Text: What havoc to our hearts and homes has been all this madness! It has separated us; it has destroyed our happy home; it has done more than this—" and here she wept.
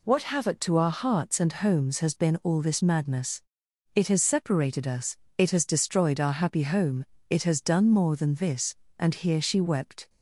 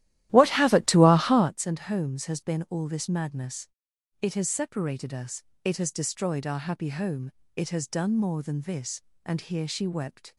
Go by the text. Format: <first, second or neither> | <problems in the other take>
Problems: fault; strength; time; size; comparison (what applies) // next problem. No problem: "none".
first | starts louder than the rest; strong; until 1.5 s; 14 dB